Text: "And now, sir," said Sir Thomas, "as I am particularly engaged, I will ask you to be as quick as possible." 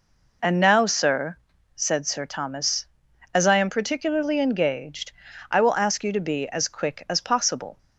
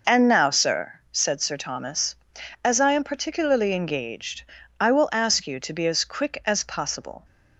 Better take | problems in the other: neither | none

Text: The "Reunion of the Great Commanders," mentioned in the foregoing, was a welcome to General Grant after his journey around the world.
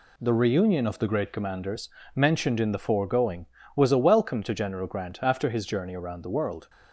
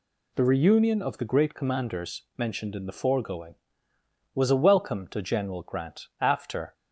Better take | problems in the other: first | stops before "his journey around the world"; at 6.7 s

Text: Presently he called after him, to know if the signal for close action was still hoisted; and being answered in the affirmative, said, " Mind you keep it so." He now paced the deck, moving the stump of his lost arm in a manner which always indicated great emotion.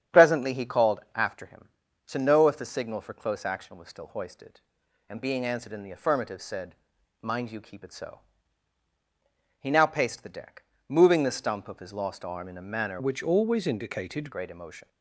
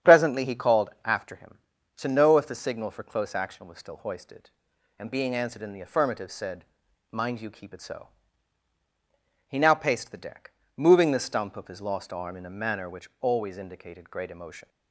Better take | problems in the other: second | starts louder than the rest; strong; until 1.2 s; 9.5 dB; strong in the second // changes voice from "which" to "indicated"; from 12.9 to 14.2 s; 1.3 s long

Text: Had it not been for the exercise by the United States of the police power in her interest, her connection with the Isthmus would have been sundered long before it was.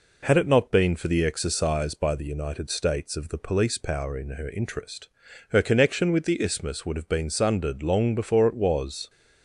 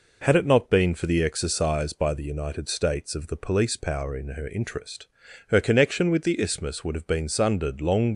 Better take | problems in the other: first | stops before "before it was"; at 8.1 s

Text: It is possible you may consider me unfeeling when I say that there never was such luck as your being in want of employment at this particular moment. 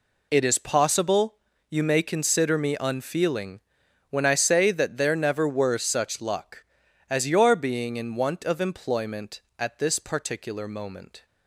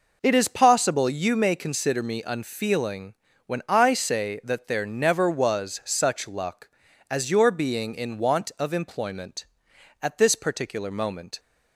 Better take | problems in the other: second | pauses between "possible" and "you"; slight; at 1.3 s; 0.34 s long // pauses between "unfeeling" and "when"; noticeable; at 3.5 s; 0.50 s long; slight in the second // says "were" for "was"; at 5.4 s

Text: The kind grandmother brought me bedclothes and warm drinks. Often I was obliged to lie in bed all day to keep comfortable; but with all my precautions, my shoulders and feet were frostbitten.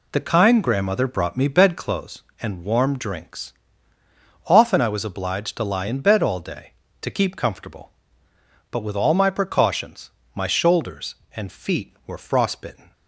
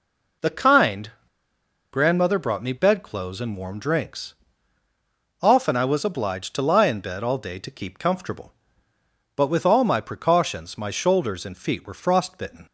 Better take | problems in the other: first | pauses between "kind" and "grandmother"; noticeable; at 1.0 s; 0.82 s long

